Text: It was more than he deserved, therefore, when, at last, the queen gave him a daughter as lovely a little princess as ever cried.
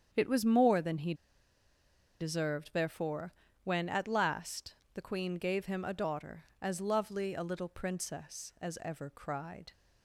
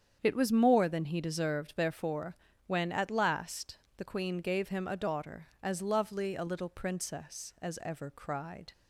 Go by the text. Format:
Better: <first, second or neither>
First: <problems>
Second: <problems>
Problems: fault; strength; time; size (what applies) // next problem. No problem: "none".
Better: second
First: starts louder than the rest; strong; until 1.1 s; 8 dB // pauses between "he" and "deserved"; at 1.1 s; 1.0 s long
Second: starts louder than the rest; strong; until 1.2 s; 8 dB